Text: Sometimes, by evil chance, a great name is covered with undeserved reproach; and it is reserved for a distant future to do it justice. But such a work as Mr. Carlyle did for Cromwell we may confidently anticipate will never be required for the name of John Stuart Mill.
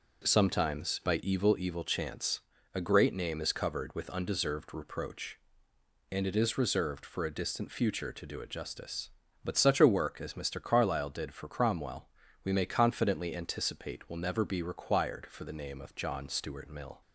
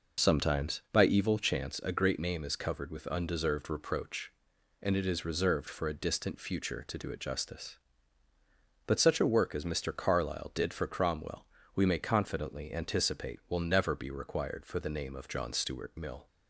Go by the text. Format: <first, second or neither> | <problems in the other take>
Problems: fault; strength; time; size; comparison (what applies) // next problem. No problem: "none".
second | says "evil" twice; at 1.5 s // pauses between "Cromwell" and "we"; at 12.0 s; 0.38 s long; slight in the second